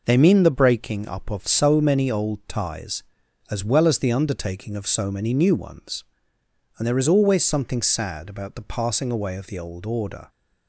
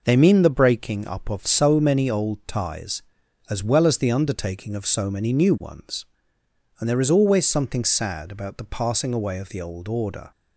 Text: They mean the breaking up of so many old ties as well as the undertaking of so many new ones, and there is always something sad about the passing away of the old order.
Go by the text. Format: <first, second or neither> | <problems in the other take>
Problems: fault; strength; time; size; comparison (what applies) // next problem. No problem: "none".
neither | none